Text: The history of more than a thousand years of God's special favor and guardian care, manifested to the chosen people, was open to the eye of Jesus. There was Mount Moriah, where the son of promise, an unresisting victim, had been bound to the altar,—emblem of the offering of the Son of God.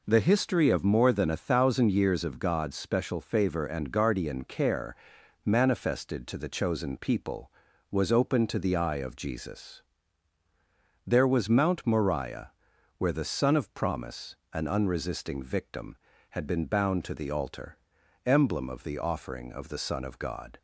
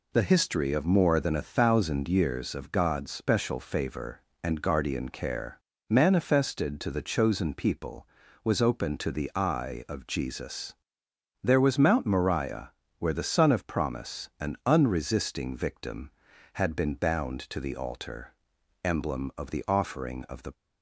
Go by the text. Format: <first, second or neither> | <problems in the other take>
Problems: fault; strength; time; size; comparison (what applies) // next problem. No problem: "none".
first | stops before "Son of God"; at 20.5 s